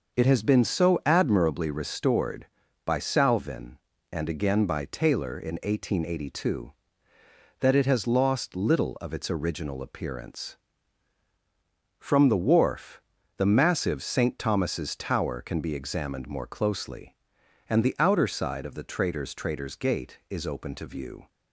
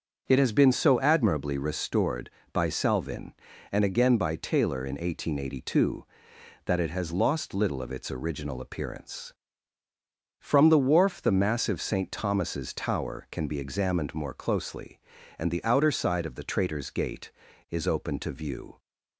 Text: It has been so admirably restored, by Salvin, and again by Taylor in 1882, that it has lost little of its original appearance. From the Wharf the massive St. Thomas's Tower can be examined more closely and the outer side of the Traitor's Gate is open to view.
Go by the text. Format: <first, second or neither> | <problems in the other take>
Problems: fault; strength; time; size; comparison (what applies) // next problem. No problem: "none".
second | starts louder than the rest; noticeable; until 1.2 s; 6 dB; also in the second // pauses between "Wharf" and "the"; slight; at 13.0 s; 0.36 s long // says "Traitor's" twice; at 19.3 s